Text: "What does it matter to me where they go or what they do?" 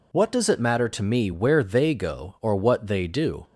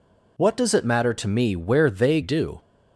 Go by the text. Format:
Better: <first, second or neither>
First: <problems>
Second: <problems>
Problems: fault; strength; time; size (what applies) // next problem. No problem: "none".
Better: first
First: none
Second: skips "go or what they"; at 2.2 s